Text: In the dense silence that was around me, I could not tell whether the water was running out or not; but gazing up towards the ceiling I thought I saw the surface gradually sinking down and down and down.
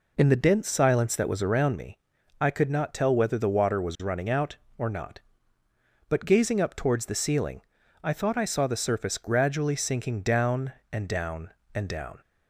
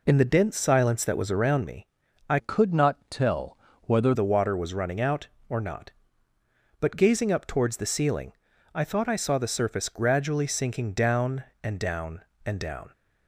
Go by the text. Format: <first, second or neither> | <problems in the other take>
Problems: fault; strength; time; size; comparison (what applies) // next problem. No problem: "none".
first | changes voice from "could" to "whether"; from 2.3 to 4.1 s; 1.8 s long // pauses between "tell" and "whether"; slight; at 3.5 s; 0.26 s long // pauses between "ceiling" and "I"; at 8.3 s; 0.42 s long; also in the first